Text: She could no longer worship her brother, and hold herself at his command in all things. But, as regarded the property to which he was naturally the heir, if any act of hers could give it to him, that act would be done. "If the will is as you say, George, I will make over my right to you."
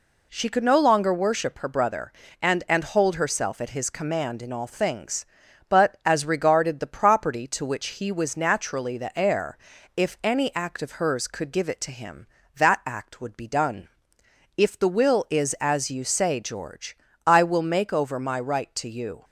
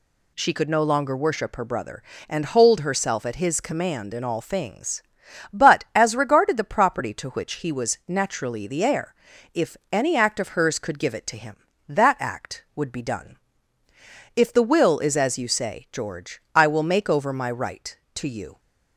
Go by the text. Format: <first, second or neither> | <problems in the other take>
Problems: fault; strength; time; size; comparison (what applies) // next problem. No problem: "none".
second | says "and" twice; at 2.6 s